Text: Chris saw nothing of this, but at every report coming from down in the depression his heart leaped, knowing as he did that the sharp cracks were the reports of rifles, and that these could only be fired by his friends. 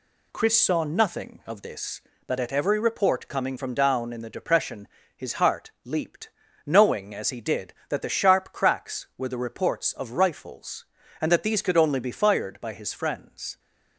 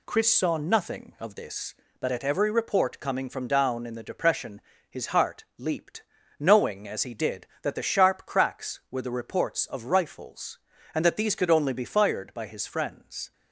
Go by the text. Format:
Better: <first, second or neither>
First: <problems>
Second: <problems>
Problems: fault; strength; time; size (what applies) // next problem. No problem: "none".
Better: neither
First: pauses between "depression" and "his"; slight; at 4.8 s; 0.30 s long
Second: pauses between "depression" and "his"; slight; at 4.5 s; 0.30 s long